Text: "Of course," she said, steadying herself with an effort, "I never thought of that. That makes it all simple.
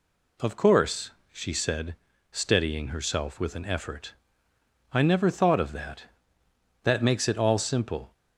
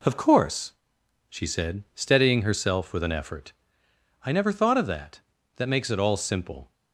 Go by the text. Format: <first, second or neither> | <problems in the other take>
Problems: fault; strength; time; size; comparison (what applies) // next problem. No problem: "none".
neither | none